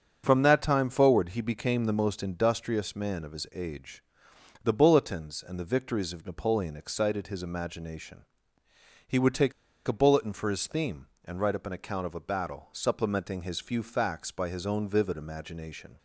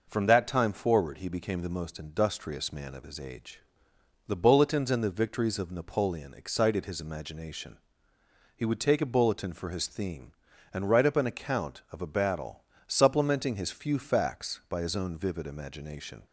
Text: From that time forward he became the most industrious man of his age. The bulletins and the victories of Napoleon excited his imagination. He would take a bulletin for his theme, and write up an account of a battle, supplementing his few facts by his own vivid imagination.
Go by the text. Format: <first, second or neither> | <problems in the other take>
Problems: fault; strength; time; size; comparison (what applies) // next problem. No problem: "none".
second | starts louder than the rest; until 1.2 s; 7 dB // pauses between "take" and "a"; slight; at 9.5 s; 0.35 s long